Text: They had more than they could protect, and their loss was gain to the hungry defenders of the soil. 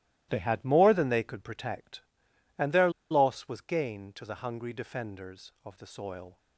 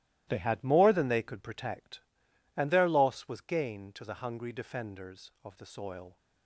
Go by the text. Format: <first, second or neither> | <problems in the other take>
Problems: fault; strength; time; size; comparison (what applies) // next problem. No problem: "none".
second | starts louder than the rest; strong; until 1.3 s; 15 dB; strong in the second // pauses between "their" and "loss"; slight; at 2.9 s; 0.20 s long